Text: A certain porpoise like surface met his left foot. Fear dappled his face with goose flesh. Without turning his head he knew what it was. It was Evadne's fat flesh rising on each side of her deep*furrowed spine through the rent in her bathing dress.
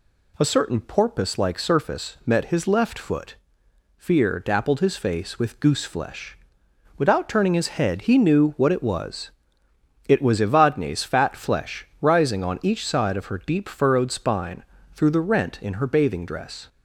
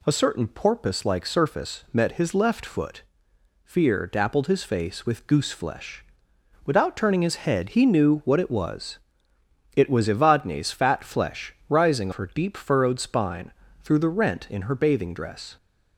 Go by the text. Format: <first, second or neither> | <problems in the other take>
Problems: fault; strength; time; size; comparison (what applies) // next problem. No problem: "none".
first | skips "on each side of"; at 12.1 s // pauses between "spine" and "through"; slight; at 13.5 s; 0.28 s long; slight in the first